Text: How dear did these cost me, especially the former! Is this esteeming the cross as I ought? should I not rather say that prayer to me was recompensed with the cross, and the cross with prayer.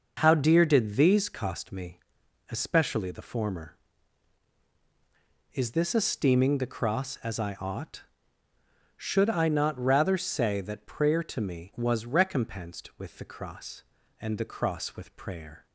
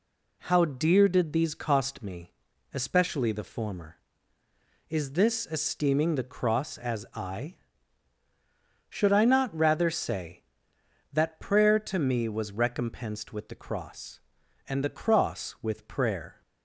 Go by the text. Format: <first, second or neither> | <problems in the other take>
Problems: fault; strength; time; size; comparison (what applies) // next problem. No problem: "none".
first | skips "ought"; at 8.2 s